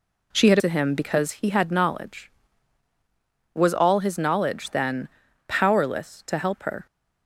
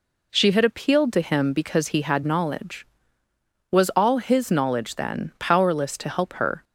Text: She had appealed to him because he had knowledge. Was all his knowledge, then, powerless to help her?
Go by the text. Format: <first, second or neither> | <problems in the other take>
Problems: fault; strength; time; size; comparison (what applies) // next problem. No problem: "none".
second | skips "appealed"; at 0.5 s